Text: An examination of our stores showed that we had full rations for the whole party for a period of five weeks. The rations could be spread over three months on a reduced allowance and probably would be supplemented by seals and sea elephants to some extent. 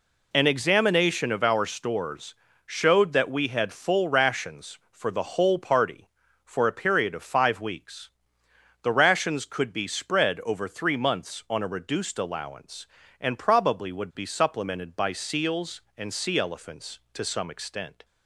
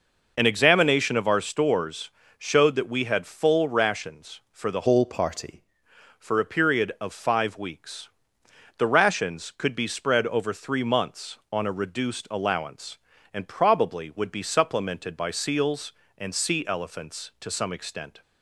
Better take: first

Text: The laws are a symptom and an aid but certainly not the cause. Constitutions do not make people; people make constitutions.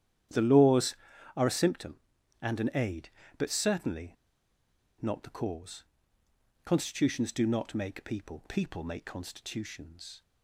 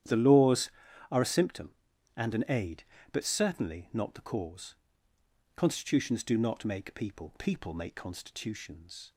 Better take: second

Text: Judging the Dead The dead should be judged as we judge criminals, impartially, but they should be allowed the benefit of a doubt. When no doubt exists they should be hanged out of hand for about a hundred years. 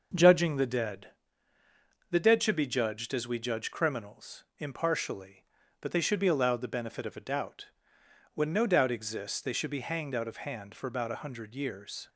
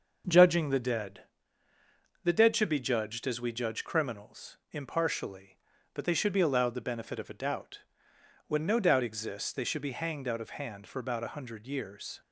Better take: neither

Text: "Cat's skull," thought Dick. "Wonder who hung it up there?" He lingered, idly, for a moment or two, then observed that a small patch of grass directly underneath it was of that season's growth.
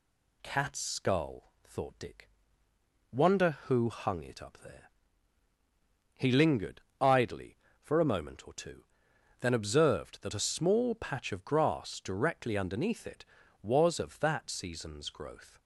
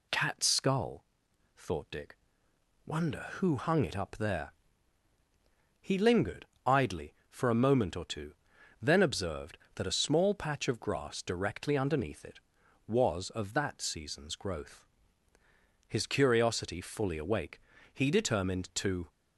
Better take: first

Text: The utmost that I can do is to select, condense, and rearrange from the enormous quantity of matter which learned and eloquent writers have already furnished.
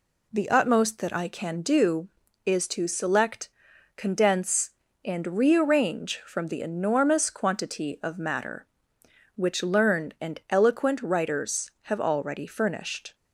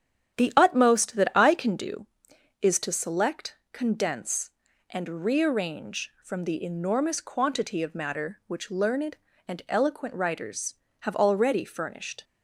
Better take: first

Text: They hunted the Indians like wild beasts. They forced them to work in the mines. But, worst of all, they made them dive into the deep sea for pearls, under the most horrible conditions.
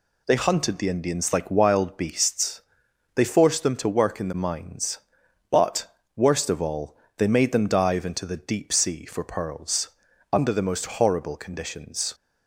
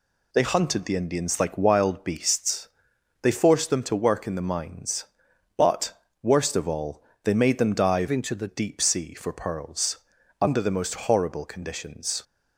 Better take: first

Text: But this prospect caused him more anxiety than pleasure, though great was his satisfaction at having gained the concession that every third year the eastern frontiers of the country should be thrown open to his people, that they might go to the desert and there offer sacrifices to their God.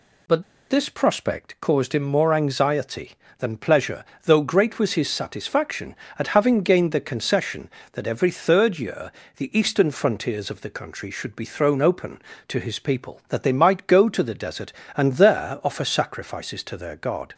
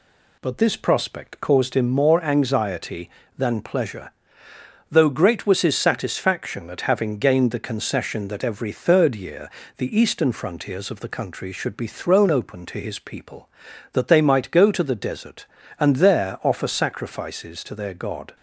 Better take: second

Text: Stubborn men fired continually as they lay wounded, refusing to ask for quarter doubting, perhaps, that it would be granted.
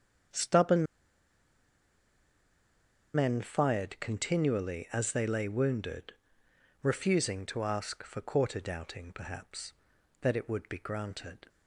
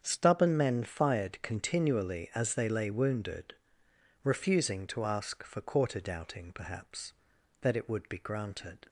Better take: second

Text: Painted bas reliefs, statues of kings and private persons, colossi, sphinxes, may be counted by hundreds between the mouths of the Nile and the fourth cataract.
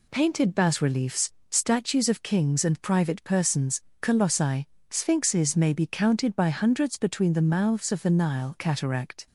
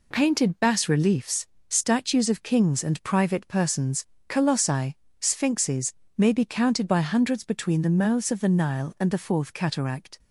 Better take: second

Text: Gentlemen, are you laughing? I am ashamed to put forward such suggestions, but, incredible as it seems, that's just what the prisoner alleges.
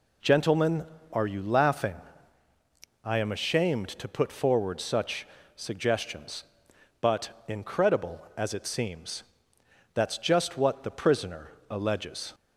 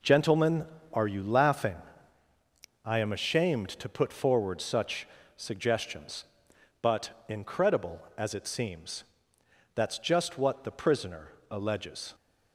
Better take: first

